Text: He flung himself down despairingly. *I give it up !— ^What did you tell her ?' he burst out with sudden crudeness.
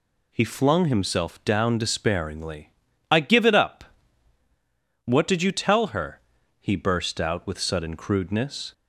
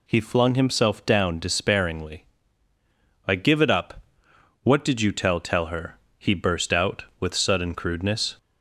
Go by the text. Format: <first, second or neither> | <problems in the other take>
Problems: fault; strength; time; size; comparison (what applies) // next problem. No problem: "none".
first | says "tell" twice; at 5.4 s